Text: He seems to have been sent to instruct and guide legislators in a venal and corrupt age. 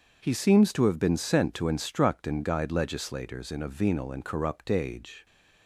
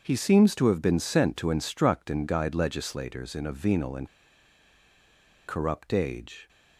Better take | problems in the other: first | starts louder than the rest; until 1.0 s; 6.5 dB // pauses between "and" and "corrupt"; strong; at 4.0 s; 1.4 s long

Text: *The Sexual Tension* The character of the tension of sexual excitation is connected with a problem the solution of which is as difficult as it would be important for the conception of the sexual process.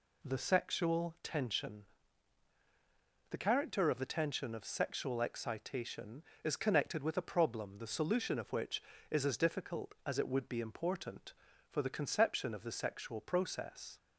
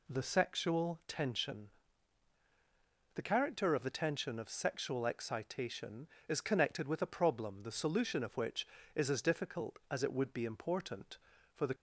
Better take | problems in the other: first | pauses between "Tension" and "The"; strong; at 1.6 s; 1.4 s long; strong in the first // stops before "conception of the sexual process"; at 11.7 s

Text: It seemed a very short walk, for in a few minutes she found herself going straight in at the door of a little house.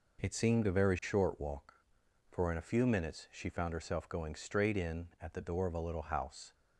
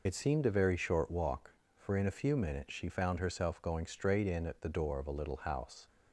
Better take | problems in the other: first | loses the start of "It"; at 0.0 s; 70 ms

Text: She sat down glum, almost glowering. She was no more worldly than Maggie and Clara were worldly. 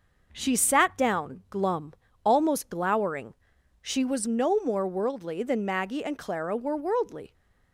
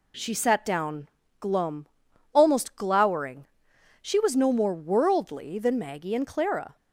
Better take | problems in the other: first | pauses between "down" and "glum"; slight; at 1.0 s; 0.32 s long // stops before "were worldly"; at 6.7 s

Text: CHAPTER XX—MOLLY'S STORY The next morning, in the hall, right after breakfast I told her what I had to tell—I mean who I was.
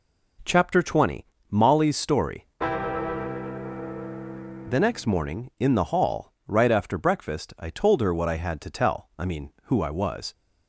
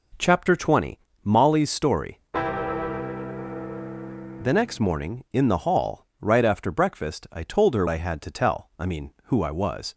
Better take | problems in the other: first | skips "what"; at 7.8 s

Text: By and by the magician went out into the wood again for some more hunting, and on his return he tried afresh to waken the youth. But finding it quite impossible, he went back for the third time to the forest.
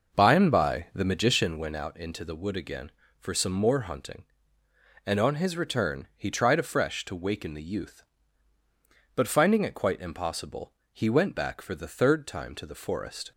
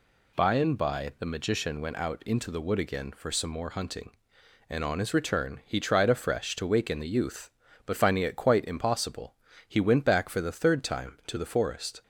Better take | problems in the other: second | starts louder than the rest; noticeable; until 1.6 s; 5.5 dB

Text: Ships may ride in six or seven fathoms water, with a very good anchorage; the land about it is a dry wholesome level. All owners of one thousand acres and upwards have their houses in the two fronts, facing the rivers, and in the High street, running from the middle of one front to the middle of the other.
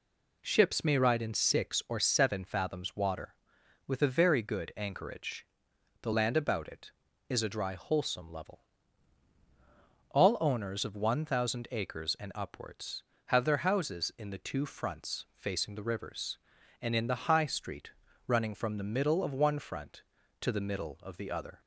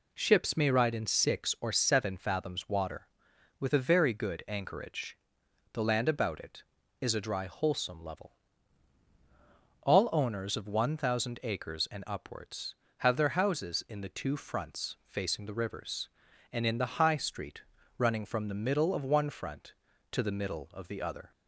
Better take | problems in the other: neither | none

